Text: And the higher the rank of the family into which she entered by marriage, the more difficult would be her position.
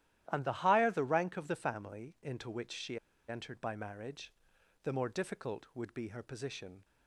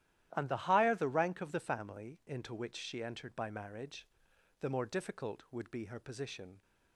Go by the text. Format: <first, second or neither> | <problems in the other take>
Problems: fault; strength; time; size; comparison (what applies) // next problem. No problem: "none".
second | starts louder than the rest; strong; until 1.2 s; 12.5 dB; strong in the second // pauses between "she" and "entered"; slight; at 2.9 s; 0.29 s long